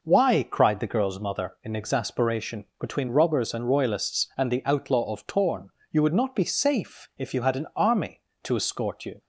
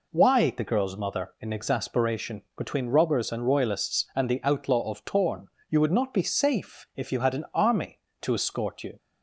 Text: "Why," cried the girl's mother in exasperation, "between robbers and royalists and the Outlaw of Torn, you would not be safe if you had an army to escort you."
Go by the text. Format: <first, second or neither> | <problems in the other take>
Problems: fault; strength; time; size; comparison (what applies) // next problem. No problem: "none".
first | skips "cried"; at 0.5 s